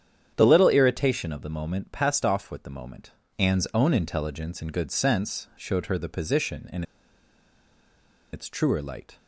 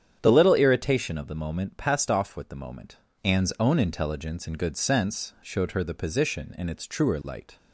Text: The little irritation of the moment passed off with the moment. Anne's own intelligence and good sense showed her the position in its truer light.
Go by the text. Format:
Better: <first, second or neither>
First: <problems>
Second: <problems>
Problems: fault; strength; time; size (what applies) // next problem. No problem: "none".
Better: second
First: starts louder than the rest; strong; until 1.3 s; 9 dB // pauses between "in" and "its"; strong; at 6.8 s; 1.4 s long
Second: starts louder than the rest; strong; until 1.2 s; 9 dB